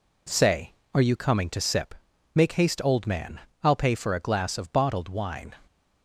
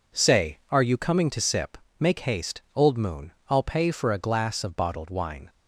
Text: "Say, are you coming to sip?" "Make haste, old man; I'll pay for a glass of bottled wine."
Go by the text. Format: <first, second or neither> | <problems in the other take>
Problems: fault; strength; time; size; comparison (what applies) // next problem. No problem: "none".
first | says "moon" for "man"; at 2.9 s